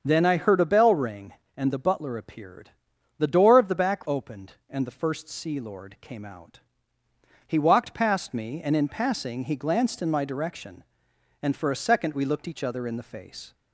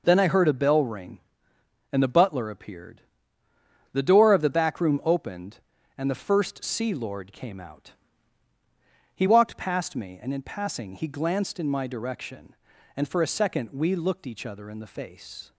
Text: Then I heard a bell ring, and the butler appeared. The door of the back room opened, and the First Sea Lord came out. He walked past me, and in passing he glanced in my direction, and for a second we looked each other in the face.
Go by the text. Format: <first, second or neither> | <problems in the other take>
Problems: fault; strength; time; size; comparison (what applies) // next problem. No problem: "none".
second | starts louder than the rest; until 1.0 s; 7 dB // skips "room"; at 4.0 s